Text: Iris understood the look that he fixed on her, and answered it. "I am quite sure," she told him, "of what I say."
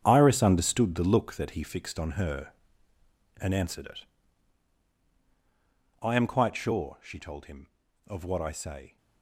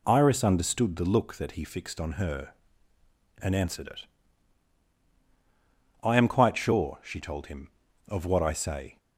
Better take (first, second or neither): second